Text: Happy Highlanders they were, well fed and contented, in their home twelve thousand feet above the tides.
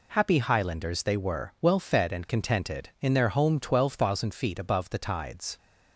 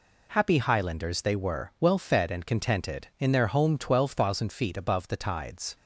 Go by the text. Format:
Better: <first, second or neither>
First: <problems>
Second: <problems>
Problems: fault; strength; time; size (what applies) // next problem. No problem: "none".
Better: neither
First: none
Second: none